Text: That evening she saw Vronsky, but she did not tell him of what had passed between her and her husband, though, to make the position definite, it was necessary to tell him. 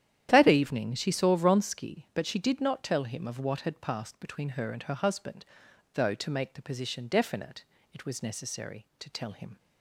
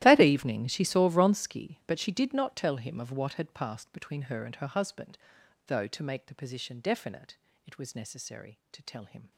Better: first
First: starts louder than the rest; strong; until 1.3 s; 10.5 dB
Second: gets quieter; strong; throughout; 19.5 dB // starts louder than the rest; strong; until 1.0 s; 14.5 dB

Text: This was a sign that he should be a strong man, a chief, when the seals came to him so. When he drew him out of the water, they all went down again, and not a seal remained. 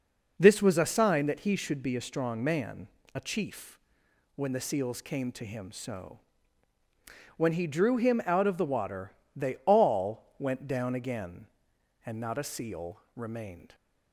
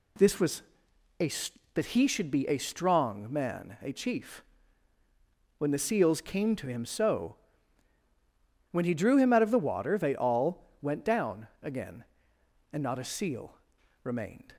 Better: first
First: pauses between "seal" and "remained"; slight; at 12.9 s; 0.16 s long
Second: pauses between "was" and "a"; noticeable; at 0.6 s; 0.58 s long // skips "sign"; at 1.5 s // pauses between "seal" and "remained"; noticeable; at 13.5 s; 0.48 s long

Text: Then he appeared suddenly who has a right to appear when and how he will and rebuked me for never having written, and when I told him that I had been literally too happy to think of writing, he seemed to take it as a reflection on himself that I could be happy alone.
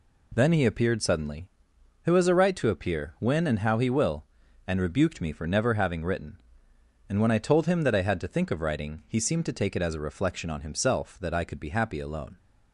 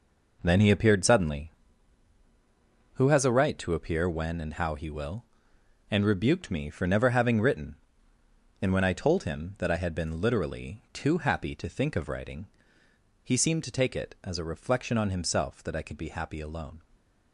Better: second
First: skips "been literally too happy"; at 8.1 s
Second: none

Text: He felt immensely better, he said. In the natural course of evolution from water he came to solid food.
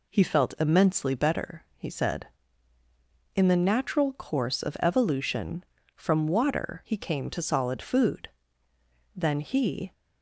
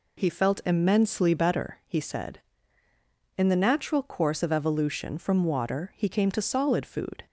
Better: second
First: goes on to say "Then he"; noticeable; from 9.1 s on; 0.78 s long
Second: none

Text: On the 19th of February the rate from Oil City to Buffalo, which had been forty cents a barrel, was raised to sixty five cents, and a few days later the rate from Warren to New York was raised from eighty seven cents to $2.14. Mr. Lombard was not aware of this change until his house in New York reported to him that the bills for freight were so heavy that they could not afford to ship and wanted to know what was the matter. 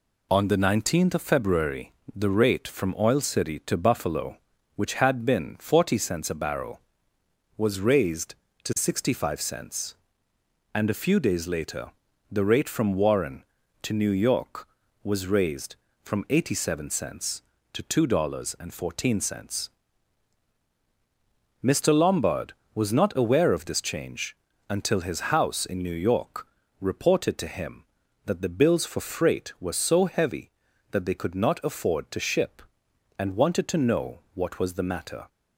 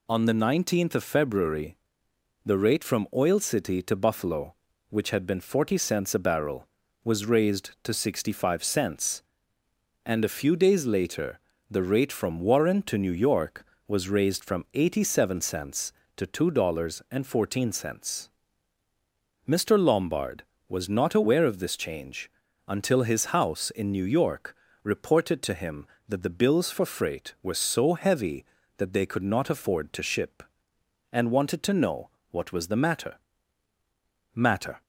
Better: first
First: pauses between "February" and "the"; slight; at 1.9 s; 0.22 s long // pauses between "later" and "the"; at 11.9 s; 0.38 s long // pauses between "change" and "until"; slight; at 24.3 s; 0.32 s long // pauses between "York" and "reported"; slight; at 26.4 s; 0.36 s long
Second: pauses between "February" and "the"; noticeable; at 1.7 s; 0.66 s long // pauses between "later" and "the"; slight; at 11.3 s; 0.30 s long // pauses between "change" and "until"; at 22.2 s; 0.38 s long // pauses between "York" and "reported"; slight; at 24.5 s; 0.26 s long // pauses between "know" and "what"; slight; at 32.0 s; 0.22 s long // says "matter" twice; at 34.3 s

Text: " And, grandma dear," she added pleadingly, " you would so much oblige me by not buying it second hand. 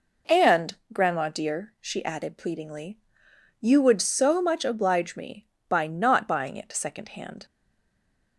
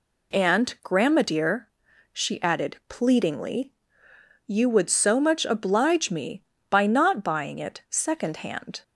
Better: second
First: stays silent after the last word; slight; from 7.4 s on; 0.9 s long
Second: none

